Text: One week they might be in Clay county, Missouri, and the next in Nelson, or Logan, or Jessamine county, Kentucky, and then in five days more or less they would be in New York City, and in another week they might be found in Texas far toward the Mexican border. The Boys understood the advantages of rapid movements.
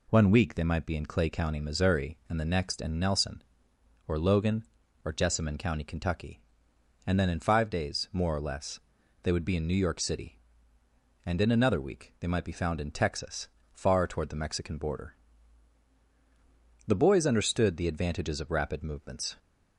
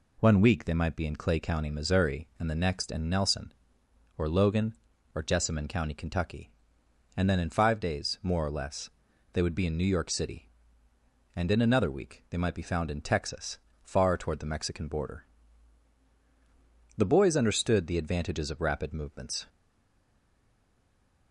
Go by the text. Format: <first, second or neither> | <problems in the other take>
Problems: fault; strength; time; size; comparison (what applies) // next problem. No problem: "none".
first | pauses between "less" and "they"; at 8.8 s; 0.44 s long; also in the first // pauses between "Texas" and "far"; slight; at 13.5 s; 0.22 s long; slight in the first // stays silent after the last word; noticeable; from 19.4 s on; 1.9 s long